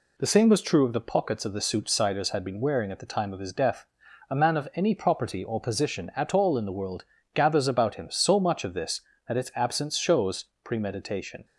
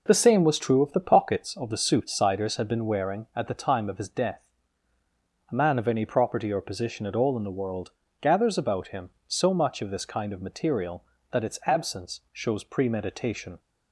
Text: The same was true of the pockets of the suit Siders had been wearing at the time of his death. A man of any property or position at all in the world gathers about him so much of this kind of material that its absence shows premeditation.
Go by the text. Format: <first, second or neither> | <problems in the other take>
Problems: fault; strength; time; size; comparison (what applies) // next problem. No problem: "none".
second | pauses between "world" and "gathers"; slight; at 7.0 s; 0.32 s long; slight in the second // skips "kind of material"; at 9.1 s // pauses between "shows" and "premeditation"; slight; at 10.4 s; 0.18 s long